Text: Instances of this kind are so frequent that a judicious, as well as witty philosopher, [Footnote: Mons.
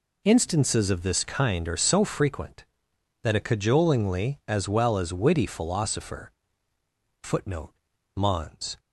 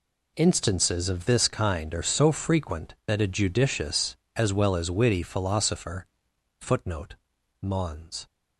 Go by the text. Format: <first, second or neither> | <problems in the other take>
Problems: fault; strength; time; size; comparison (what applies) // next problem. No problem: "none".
second | says "cajolingly" for "judicious"; at 3.3 s